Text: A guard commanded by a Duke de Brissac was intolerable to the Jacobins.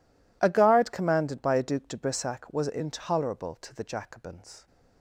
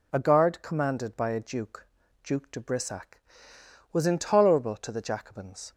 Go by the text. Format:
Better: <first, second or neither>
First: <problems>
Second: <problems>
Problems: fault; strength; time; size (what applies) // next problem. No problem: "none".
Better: first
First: none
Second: says "Duke" twice; at 2.2 s